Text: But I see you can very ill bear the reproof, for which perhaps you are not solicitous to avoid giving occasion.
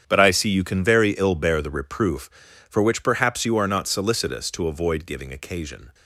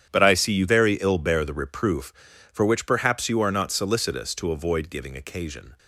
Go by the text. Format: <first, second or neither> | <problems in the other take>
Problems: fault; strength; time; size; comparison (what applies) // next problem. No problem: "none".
first | starts louder than the rest; strong; until 1.1 s; 9.5 dB; strong in the first // skips "can"; at 0.6 s